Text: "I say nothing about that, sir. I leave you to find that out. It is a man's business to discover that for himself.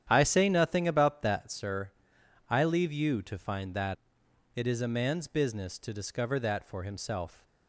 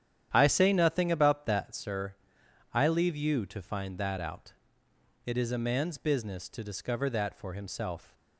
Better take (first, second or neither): second